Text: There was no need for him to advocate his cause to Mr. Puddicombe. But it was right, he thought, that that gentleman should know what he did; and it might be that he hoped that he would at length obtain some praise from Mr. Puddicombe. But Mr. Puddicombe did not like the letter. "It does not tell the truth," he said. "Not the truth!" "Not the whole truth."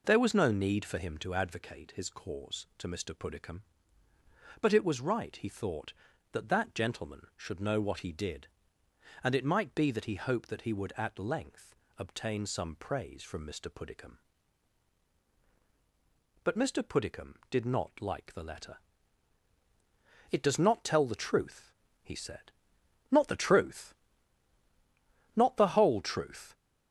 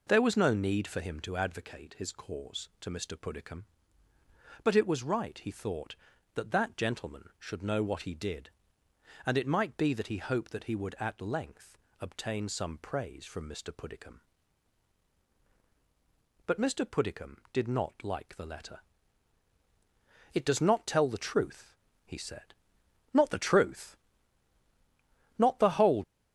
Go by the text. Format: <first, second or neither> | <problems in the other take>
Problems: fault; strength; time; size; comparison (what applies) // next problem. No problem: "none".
first | pauses between "length" and "obtain"; slight; at 11.7 s; 0.24 s long; slight in the first // stops before "truth"; at 26.0 s